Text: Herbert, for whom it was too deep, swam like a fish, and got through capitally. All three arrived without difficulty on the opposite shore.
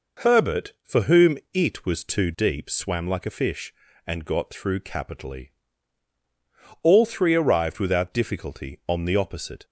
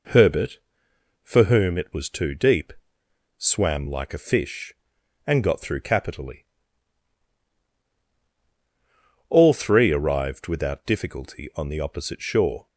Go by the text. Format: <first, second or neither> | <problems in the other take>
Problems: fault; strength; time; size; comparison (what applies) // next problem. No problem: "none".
second | pauses between "whom" and "it"; slight; at 1.3 s; 0.16 s long // stops before "shore"; at 9.6 s